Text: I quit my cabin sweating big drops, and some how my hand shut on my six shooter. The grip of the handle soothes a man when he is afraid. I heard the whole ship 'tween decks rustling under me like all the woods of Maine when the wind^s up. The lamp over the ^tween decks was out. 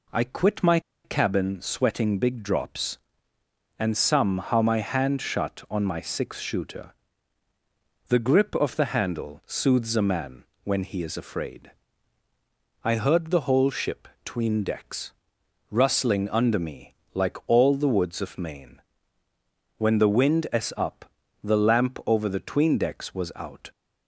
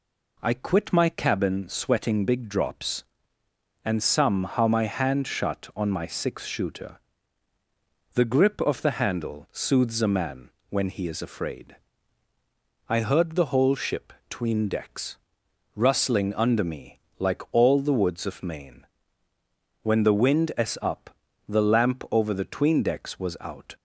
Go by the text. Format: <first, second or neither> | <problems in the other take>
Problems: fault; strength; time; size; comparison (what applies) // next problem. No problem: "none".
second | pauses between "my" and "cabin"; slight; at 0.7 s; 0.24 s long // pauses between "man" and "when"; slight; at 10.4 s; 0.18 s long; slight in the second // pauses between "ship" and "tween"; slight; at 14.0 s; 0.16 s long; slight in the second // pauses between "decks" and "rustling"; noticeable; at 15.1 s; 0.58 s long; noticeable in the second // pauses between "me" and "like"; slight; at 16.9 s; 0.18 s long; slight in the second // pauses between "Maine" and "when"; noticeable; at 18.8 s; 0.98 s long; noticeable in the second